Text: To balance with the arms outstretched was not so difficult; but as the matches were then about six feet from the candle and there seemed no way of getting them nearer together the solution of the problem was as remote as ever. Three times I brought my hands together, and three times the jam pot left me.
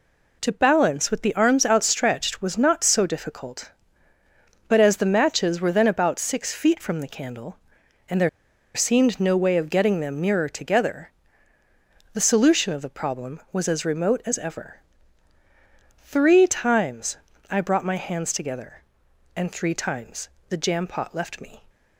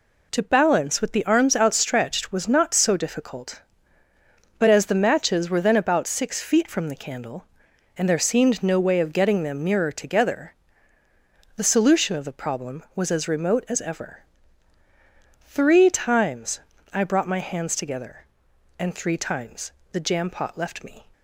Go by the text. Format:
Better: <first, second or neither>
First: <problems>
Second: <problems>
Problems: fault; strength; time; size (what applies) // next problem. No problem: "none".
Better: second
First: pauses between "there" and "seemed"; noticeable; at 8.2 s; 0.46 s long // pauses between "together" and "the"; at 11.0 s; 1.0 s long // pauses between "times" and "I"; slight; at 17.1 s; 0.34 s long // pauses between "times" and "the"; slight; at 20.2 s; 0.22 s long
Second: pauses between "together" and "the"; at 10.5 s; 1.0 s long // pauses between "times" and "I"; slight; at 16.5 s; 0.34 s long // pauses between "times" and "the"; slight; at 19.7 s; 0.22 s long